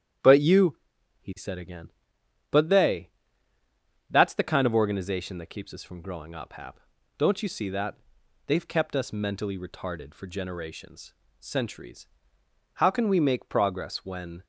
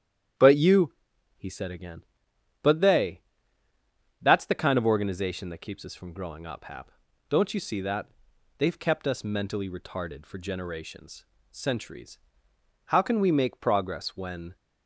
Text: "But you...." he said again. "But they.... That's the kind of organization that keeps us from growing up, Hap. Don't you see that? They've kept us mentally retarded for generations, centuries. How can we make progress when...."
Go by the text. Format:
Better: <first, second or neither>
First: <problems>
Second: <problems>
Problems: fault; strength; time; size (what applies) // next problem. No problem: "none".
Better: neither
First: starts louder than the rest; strong; until 1.7 s; 10 dB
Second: starts louder than the rest; strong; until 1.8 s; 10 dB